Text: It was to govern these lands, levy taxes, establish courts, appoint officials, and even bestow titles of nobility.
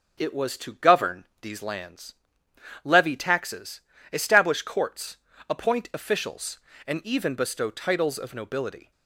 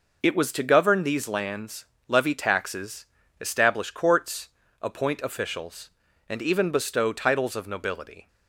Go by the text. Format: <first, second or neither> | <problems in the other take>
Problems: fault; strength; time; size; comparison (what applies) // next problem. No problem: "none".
second | starts louder than the rest; until 1.7 s; 7 dB // pauses between "govern" and "these"; slight; at 1.2 s; 0.18 s long